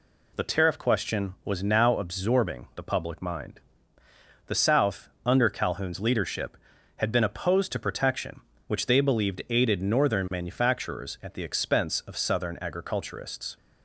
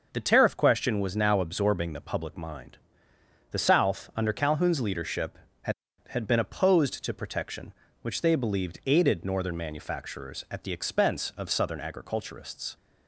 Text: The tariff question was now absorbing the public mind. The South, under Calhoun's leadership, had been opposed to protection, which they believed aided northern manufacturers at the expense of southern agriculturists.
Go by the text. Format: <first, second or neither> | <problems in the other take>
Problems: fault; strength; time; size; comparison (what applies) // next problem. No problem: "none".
first | starts louder than the rest; noticeable; until 1.1 s; 6 dB // says "had" twice; at 6.0 s